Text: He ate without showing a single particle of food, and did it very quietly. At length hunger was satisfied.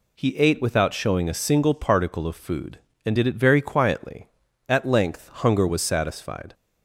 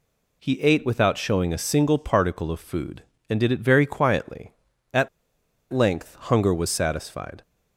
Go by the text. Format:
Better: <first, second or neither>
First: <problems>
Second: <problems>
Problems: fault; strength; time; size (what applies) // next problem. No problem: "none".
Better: first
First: none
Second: pauses between "At" and "length"; noticeable; at 5.0 s; 0.65 s long